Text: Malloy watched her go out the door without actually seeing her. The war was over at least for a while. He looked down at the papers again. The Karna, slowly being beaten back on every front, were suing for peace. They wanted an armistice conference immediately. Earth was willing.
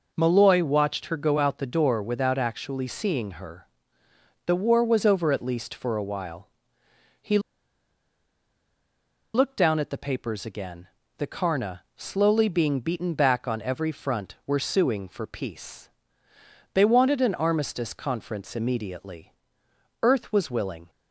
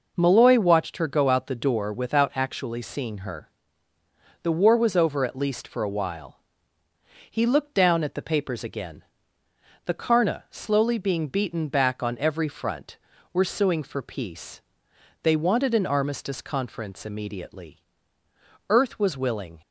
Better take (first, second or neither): second